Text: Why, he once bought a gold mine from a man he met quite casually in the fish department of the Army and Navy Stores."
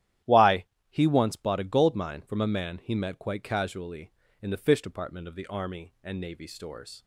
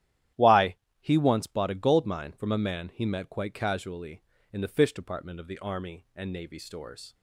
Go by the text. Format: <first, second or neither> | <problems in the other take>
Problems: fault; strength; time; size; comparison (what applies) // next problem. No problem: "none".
neither | starts louder than the rest; strong; the same in both